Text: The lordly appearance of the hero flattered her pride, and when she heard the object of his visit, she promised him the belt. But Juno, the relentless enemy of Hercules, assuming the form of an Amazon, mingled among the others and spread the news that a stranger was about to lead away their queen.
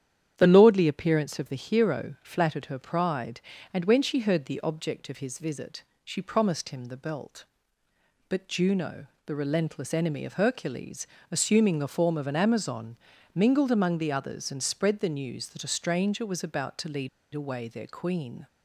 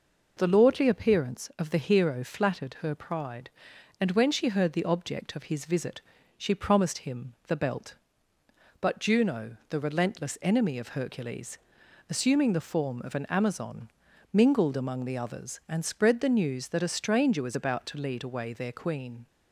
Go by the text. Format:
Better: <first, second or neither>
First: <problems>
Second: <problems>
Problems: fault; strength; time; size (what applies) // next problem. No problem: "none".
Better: second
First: starts louder than the rest; strong; until 1.3 s; 9.5 dB // pauses between "lead" and "away"; slight; at 17.0 s; 0.26 s long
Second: none